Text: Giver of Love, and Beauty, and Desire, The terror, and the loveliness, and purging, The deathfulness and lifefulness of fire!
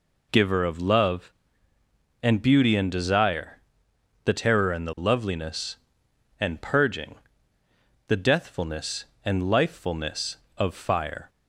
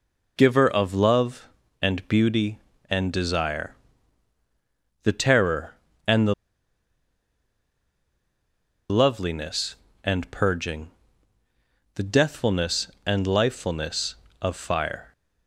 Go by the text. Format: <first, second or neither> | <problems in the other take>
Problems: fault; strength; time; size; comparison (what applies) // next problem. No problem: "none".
first | pauses between "the" and "loveliness"; strong; at 6.3 s; 2.5 s long